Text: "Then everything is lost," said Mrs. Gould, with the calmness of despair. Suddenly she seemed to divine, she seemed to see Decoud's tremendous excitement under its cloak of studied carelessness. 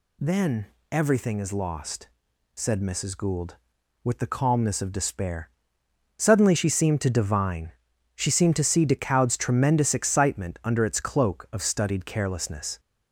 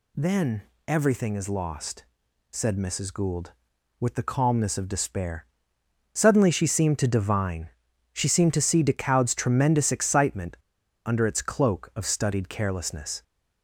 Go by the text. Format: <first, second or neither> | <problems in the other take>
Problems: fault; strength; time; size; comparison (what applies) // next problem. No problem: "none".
first | pauses between "Then" and "everything"; slight; at 0.6 s; 0.26 s long; slight in the first // pauses between "excitement" and "under"; noticeable; at 10.5 s; 0.50 s long